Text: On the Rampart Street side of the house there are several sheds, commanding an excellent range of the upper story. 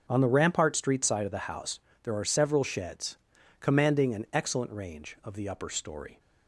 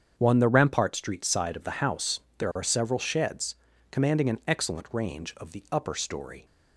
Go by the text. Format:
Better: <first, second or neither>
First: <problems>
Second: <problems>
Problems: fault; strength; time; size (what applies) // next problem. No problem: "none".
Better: first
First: starts louder than the rest; until 1.0 s; 6 dB // pauses between "house" and "there"; slight; at 1.8 s; 0.22 s long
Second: starts louder than the rest; strong; until 1.1 s; 7.5 dB // says "One" for "On"; at 0.1 s // pauses between "house" and "there"; slight; at 2.2 s; 0.18 s long